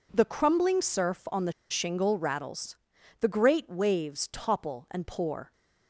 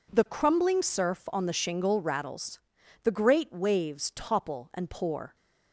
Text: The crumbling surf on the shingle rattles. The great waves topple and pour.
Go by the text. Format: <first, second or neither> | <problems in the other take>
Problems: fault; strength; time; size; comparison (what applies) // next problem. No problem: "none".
second | pauses between "the" and "shingle"; slight; at 1.5 s; 0.18 s long